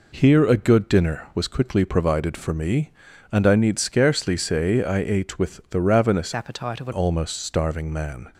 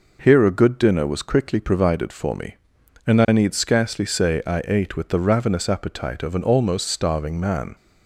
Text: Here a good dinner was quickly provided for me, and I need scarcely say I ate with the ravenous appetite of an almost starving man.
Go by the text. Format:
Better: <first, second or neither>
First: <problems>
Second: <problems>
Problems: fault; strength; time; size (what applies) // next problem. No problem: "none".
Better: second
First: changes voice from "appetite" to "an"; from 6.3 to 6.9 s; 0.6 s long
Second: none